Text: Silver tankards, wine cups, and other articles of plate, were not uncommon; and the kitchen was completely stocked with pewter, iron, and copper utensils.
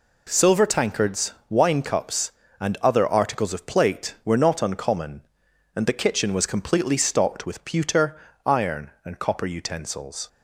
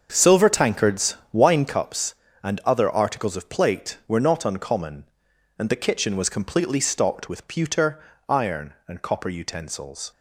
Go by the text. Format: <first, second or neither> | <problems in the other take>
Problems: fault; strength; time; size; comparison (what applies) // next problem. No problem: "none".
first | starts louder than the rest; until 1.9 s; 6.5 dB